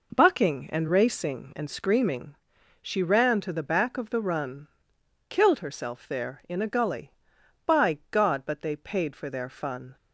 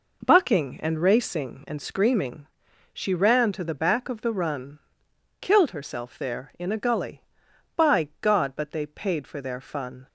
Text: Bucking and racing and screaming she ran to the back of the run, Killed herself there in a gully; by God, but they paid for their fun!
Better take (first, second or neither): neither